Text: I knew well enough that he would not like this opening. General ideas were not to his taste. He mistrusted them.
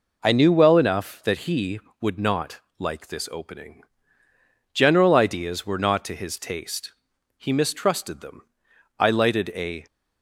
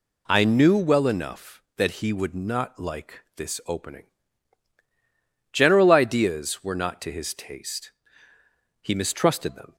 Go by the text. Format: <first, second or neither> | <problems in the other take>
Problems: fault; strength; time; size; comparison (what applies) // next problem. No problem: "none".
second | pauses between "not" and "like"; slight; at 2.5 s; 0.20 s long // goes on to say "I lighted a"; noticeable; from 8.9 s on; 0.88 s long